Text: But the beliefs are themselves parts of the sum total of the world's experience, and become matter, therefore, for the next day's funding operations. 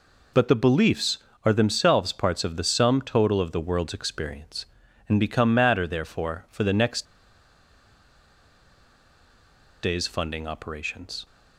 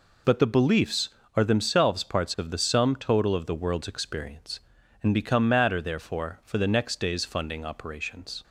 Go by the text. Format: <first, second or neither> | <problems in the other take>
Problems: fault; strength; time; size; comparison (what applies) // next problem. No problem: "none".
second | pauses between "next" and "day's"; strong; at 7.0 s; 2.7 s long